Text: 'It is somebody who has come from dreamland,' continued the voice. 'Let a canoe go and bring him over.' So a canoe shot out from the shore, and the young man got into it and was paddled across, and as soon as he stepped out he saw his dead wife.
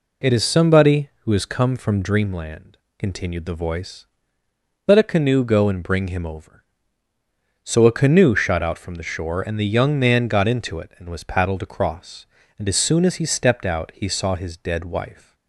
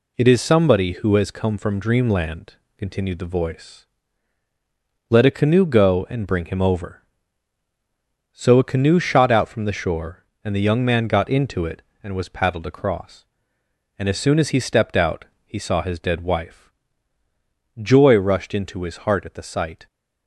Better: first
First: none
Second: pauses between "out" and "he"; slight; at 15.2 s; 0.20 s long // goes on to say "Joy rushed into his heart at the sight"; strong; from 17.8 s on; 2.0 s long

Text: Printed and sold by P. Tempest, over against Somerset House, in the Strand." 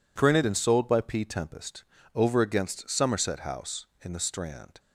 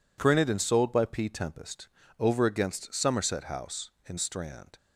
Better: first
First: none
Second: skips "the"; at 4.1 s

